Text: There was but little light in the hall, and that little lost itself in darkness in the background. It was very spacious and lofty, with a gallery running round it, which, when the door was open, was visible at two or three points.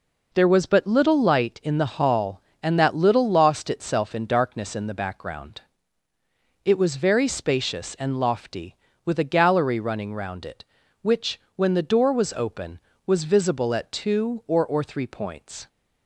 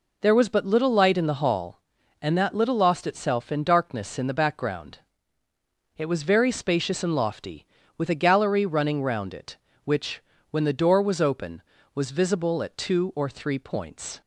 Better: second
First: says "or" twice; at 14.6 s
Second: none

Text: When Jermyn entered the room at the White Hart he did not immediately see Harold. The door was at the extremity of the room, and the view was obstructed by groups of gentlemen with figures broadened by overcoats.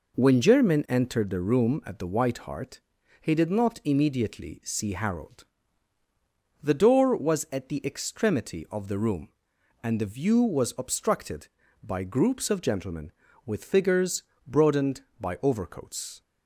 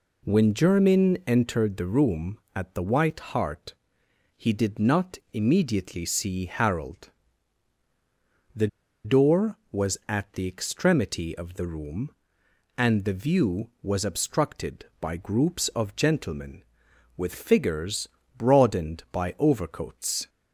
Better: first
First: pauses between "Hart" and "he"; at 2.8 s; 0.40 s long // pauses between "figures" and "broadened"; slight; at 14.2 s; 0.24 s long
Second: pauses between "Hart" and "he"; noticeable; at 3.7 s; 0.64 s long // pauses between "not" and "immediately"; slight; at 5.1 s; 0.16 s long // pauses between "The" and "door"; at 8.6 s; 0.36 s long // pauses between "figures" and "broadened"; slight; at 18.0 s; 0.28 s long

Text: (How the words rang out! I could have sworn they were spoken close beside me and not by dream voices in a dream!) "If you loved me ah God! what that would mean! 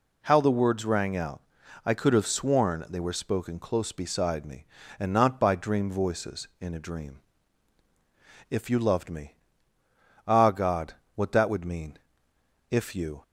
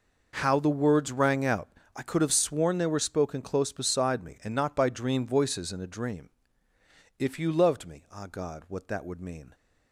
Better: second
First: pauses between "me" and "ah"; noticeable; at 9.3 s; 0.90 s long // goes on to say "If you"; from 12.6 s on; 0.54 s long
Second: none

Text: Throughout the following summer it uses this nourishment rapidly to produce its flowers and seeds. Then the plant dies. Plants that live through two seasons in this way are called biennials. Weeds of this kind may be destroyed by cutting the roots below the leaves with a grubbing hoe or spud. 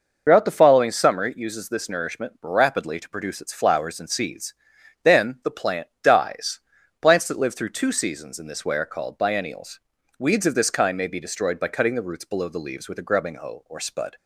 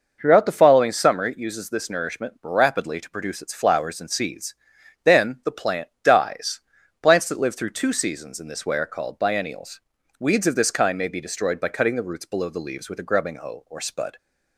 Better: second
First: loses the start of "Throughout"; at 0.2 s; 85 ms // pauses between "plant" and "dies"; slight; at 5.8 s; 0.16 s long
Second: pauses between "plant" and "dies"; slight; at 5.8 s; 0.16 s long

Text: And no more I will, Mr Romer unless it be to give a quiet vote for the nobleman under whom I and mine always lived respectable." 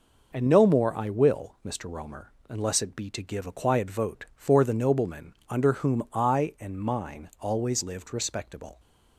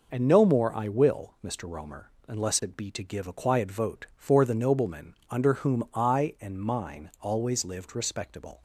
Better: neither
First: pauses between "Romer" and "unless"; slight; at 2.3 s; 0.18 s long // pauses between "nobleman" and "under"; slight; at 5.3 s; 0.16 s long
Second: pauses between "Romer" and "unless"; slight; at 2.0 s; 0.18 s long // pauses between "nobleman" and "under"; slight; at 5.1 s; 0.16 s long

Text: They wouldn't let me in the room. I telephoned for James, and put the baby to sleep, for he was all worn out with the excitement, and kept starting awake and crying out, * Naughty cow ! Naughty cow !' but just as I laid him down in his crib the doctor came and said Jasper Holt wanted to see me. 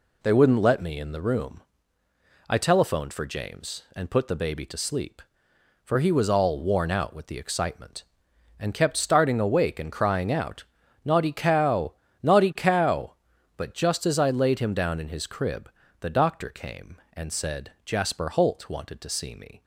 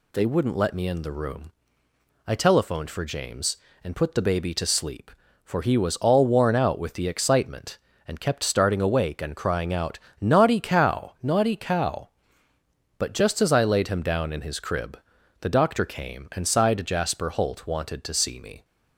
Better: first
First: pauses between "crib" and "the"; slight; at 15.6 s; 0.30 s long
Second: pauses between "crib" and "the"; at 14.9 s; 0.40 s long // says "sighed" for "said"; at 16.4 s

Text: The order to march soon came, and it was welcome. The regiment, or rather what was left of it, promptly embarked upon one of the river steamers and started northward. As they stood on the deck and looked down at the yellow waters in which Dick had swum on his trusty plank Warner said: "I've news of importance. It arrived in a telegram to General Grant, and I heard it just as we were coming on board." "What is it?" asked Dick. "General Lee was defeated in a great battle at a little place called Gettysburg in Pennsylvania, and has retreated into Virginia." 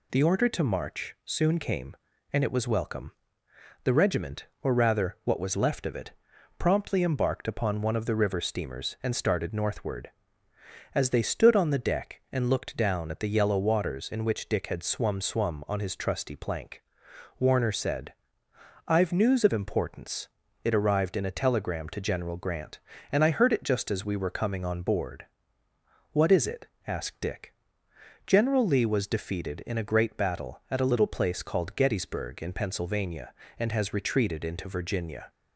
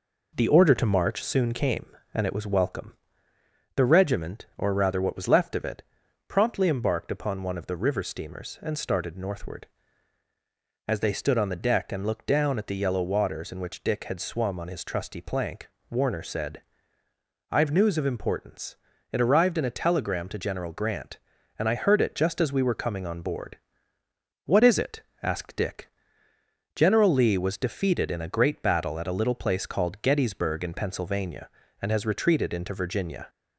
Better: second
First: says "swum" twice; at 15.2 s // pauses between "plank" and "Warner"; noticeable; at 16.8 s; 0.56 s long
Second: pauses between "plank" and "Warner"; slight; at 15.6 s; 0.20 s long

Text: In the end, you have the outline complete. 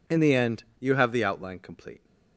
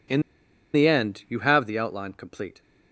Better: first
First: none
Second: pauses between "In" and "the"; noticeable; at 0.2 s; 0.52 s long

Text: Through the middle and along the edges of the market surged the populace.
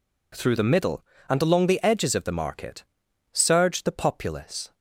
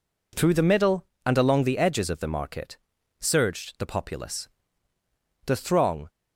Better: first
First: pauses between "market" and "surged"; noticeable; at 2.8 s; 0.48 s long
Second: pauses between "market" and "surged"; at 2.7 s; 0.44 s long // goes on to say "The throng"; noticeable; from 5.4 s on; 0.62 s long

